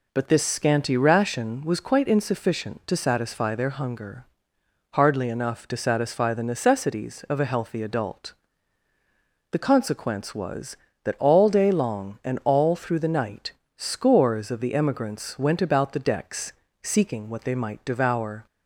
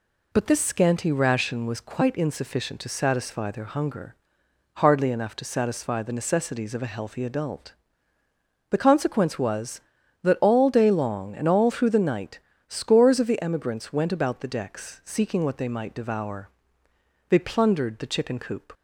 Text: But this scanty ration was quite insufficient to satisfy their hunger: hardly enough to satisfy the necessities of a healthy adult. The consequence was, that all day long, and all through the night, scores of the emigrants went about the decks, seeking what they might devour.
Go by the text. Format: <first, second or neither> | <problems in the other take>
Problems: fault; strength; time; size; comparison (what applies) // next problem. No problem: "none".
first | goes on to say "They plundered the chicken coop"; from 17.2 s on; 1.4 s long